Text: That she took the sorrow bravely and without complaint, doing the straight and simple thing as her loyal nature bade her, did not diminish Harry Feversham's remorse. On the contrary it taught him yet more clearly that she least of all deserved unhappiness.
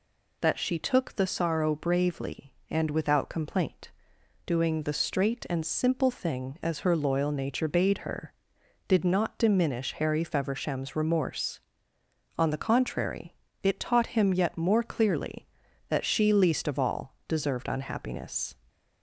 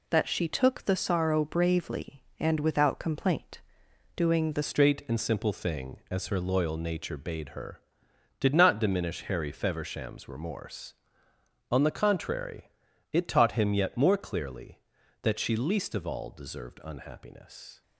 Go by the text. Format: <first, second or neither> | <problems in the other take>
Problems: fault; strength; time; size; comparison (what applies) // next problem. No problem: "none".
first | changes voice at "straight"; from 4.6 s on; 13.2 s long // pauses between "contrary" and "it"; at 12.6 s; 0.44 s long; slight in the first